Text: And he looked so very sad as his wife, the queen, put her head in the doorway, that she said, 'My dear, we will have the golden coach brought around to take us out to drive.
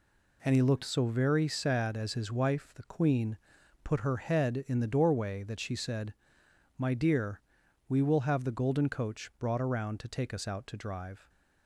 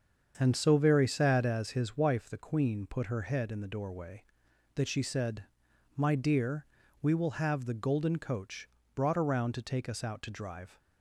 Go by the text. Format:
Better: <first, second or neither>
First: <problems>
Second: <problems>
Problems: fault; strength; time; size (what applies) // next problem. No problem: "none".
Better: first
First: none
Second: starts louder than the rest; strong; until 1.3 s; 7 dB // skips "he looked"; at 0.5 s // pauses between "coach" and "brought"; slight; at 8.6 s; 0.26 s long